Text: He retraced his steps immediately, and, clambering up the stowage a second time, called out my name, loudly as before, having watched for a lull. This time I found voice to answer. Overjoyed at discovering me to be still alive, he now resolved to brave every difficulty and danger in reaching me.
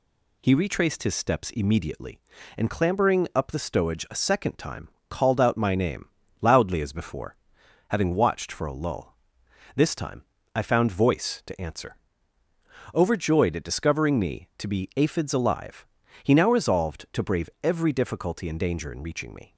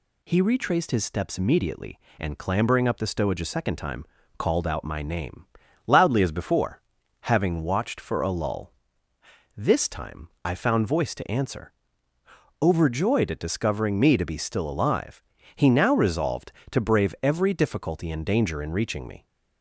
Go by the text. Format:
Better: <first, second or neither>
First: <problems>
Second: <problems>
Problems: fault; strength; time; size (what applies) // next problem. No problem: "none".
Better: second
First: pauses between "time" and "I"; slight; at 10.2 s; 0.32 s long // says "aphids" for "still"; at 14.9 s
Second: pauses between "time" and "I"; slight; at 10.2 s; 0.16 s long